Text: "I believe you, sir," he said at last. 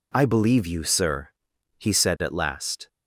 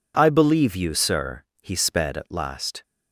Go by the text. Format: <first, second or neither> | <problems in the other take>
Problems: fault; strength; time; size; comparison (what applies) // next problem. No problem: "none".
first | says "sped" for "said"; at 1.7 s